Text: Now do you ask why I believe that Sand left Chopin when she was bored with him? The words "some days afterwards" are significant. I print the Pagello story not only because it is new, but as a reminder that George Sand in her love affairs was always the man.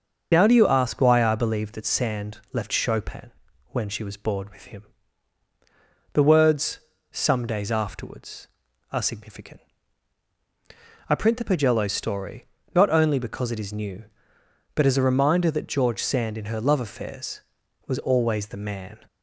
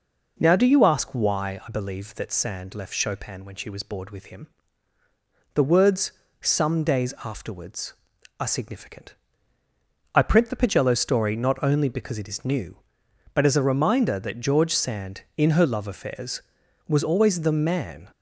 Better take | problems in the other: second | loses the start of "Now"; at 0.3 s; 35 ms // starts louder than the rest; until 1.3 s; 6.5 dB // pauses between "Sand" and "left"; slight; at 2.3 s; 0.16 s long // pauses between "Chopin" and "when"; at 3.3 s; 0.40 s long // pauses between "words" and "some"; slight; at 6.8 s; 0.30 s long; slight in the second // pauses between "story" and "not"; slight; at 12.4 s; 0.30 s long

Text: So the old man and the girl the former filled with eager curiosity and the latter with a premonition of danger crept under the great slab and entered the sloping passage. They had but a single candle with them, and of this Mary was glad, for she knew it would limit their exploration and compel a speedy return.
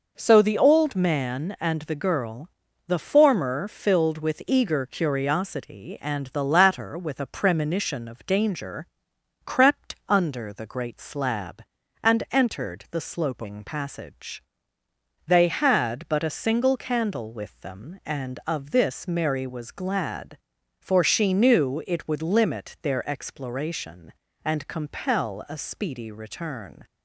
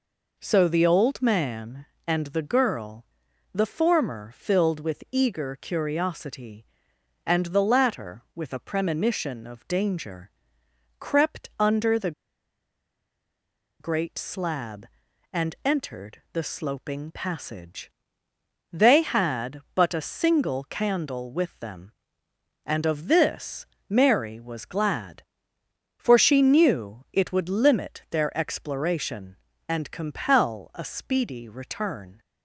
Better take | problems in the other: first | pauses between "girl" and "the"; noticeable; at 3.0 s; 0.48 s long; also in the first // pauses between "danger" and "crept"; noticeable; at 10.2 s; 0.70 s long; noticeable in the first // pauses between "the" and "great"; strong; at 12.1 s; 1.6 s long // pauses between "this" and "Mary"; slight; at 23.6 s; 0.22 s long

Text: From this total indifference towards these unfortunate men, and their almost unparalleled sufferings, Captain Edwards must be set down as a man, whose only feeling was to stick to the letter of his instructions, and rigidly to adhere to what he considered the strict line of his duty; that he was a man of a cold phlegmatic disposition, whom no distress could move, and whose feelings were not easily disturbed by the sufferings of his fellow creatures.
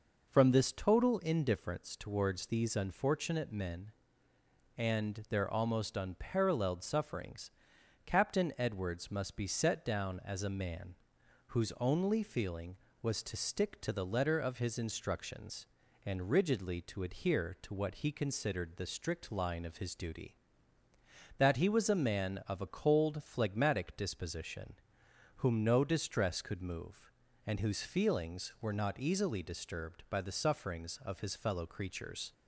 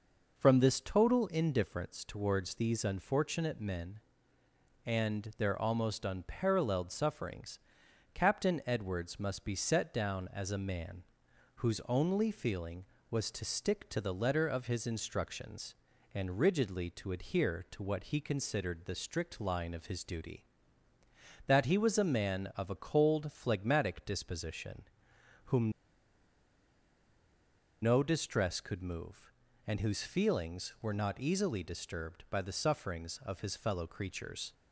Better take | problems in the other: first | pauses between "whom" and "no"; strong; at 25.7 s; 2.1 s long

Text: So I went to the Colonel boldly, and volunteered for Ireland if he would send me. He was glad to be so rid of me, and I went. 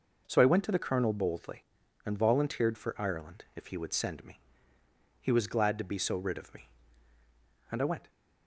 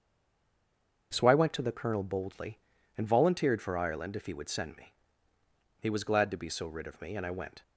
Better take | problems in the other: first | stays silent before the first word; until 1.1 s; 1.1 s long // starts louder than the rest; until 2.1 s; 6.5 dB

